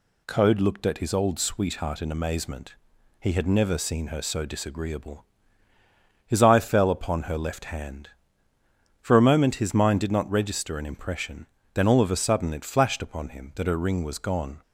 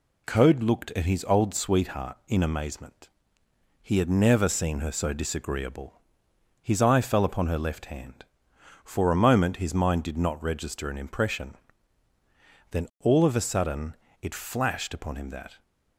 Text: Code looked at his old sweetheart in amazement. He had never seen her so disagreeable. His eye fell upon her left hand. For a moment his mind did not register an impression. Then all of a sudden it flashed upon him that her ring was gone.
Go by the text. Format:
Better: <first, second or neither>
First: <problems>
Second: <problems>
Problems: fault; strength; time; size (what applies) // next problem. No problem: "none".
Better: first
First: none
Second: pauses between "sudden" and "it"; slight; at 13.9 s; 0.26 s long // stops before "her ring was gone"; at 15.6 s